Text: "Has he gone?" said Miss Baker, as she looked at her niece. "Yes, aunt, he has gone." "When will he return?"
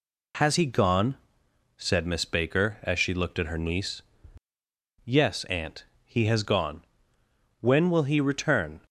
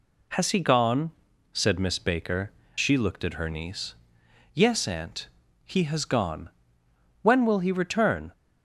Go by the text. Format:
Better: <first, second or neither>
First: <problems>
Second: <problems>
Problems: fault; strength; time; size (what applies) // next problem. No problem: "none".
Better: first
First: none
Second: skips "as"; at 2.6 s